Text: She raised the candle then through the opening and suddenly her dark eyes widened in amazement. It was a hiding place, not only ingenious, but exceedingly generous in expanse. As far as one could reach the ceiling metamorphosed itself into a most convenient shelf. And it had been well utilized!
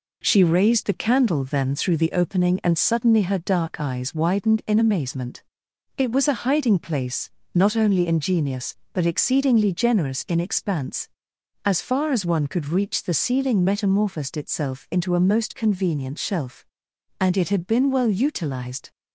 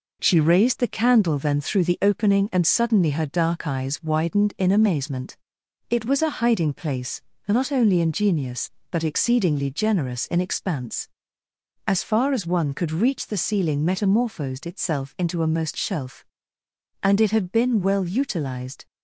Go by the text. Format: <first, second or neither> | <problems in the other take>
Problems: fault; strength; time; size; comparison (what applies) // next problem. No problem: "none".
first | skips "convenient"; at 15.7 s